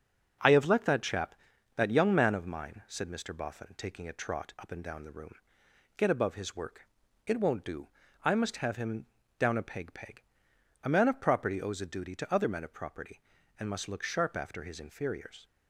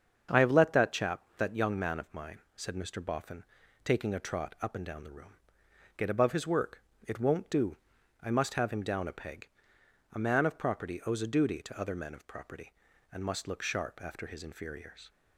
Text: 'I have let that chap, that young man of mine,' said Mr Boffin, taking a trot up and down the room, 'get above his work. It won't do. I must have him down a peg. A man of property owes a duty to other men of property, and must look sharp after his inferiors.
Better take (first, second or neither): second